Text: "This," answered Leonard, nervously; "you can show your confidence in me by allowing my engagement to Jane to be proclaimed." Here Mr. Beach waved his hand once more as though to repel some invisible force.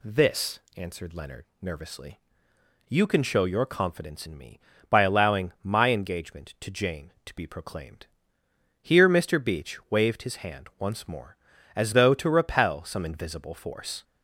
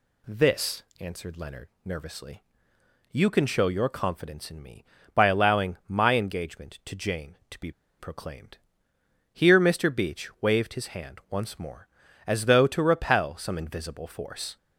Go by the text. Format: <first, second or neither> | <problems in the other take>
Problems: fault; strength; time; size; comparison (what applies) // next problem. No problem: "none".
first | pauses between "be" and "proclaimed"; slight; at 7.6 s; 0.29 s long